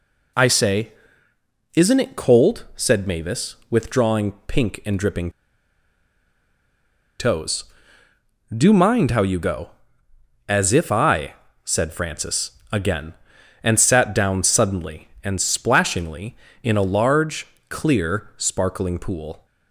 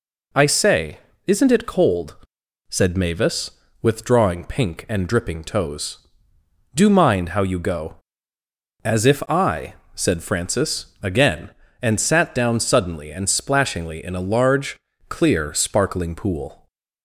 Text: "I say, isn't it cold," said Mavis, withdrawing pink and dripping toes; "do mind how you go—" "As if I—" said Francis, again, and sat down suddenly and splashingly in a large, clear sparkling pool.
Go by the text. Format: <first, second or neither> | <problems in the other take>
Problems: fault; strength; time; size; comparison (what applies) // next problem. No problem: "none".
second | pauses between "withdrawing" and "pink"; slight; at 4.3 s; 0.16 s long // pauses between "dripping" and "toes"; strong; at 5.2 s; 1.9 s long